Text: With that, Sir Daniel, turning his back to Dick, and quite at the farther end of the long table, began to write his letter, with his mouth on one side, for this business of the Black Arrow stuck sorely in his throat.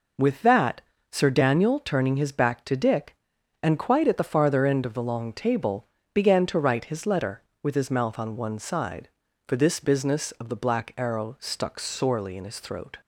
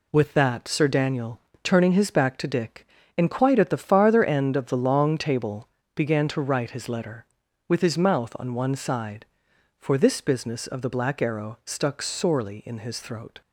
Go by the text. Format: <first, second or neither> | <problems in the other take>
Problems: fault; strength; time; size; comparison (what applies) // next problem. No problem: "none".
neither | none